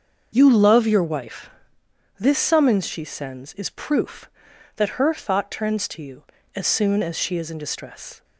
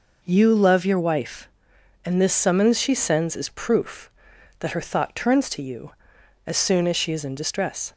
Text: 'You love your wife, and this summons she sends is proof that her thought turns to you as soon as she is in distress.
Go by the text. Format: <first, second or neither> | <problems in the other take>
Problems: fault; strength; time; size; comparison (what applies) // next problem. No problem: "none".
second | starts louder than the rest; until 1.3 s; 6.5 dB // skips "and"; at 1.8 s